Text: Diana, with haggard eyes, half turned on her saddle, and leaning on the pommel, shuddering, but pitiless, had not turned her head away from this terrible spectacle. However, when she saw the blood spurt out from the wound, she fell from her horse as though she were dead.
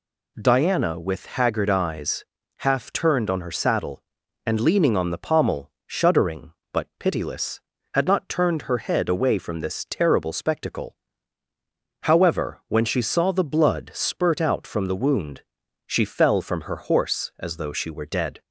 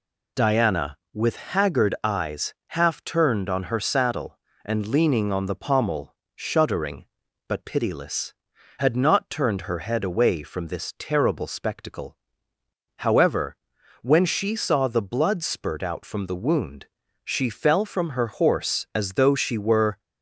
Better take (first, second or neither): first